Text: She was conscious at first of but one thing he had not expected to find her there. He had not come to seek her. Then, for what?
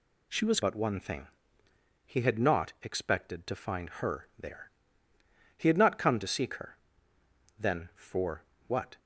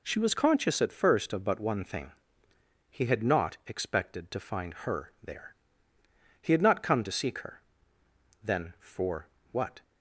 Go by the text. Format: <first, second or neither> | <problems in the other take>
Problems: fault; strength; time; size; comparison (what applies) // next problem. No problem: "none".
second | skips "conscious at first of"; at 0.6 s // pauses between "thing" and "he"; noticeable; at 1.2 s; 0.80 s long; noticeable in the second // pauses between "for" and "what"; slight; at 8.4 s; 0.24 s long; slight in the second